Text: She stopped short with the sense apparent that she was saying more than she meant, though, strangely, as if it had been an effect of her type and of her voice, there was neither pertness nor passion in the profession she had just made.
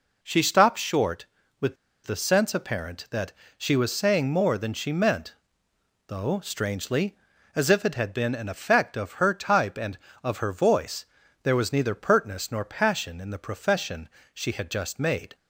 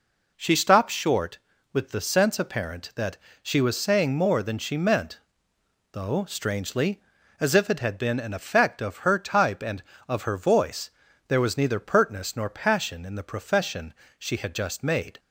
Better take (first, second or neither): second